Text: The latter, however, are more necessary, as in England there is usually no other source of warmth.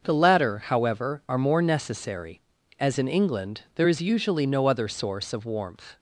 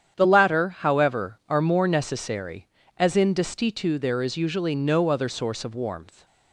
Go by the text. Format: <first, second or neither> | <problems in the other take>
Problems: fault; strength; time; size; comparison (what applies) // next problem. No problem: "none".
first | starts louder than the rest; strong; until 1.1 s; 9 dB; also in the first // says "Destitu" for "England"; at 3.3 s